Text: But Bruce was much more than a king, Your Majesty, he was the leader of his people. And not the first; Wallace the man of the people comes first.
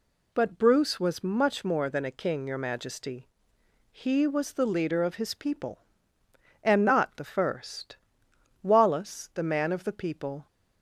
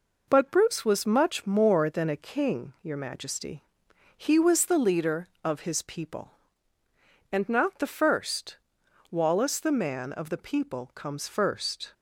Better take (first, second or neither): second